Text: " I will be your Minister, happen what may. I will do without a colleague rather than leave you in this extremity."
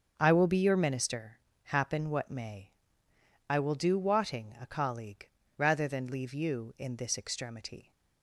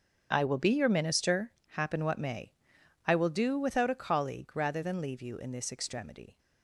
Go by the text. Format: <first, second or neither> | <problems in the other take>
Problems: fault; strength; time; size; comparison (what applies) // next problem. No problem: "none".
second | starts louder than the rest; until 1.1 s; 6.5 dB; also in the second // says "wotting" for "without"; at 3.9 s // pauses between "colleague" and "rather"; slight; at 5.2 s; 0.30 s long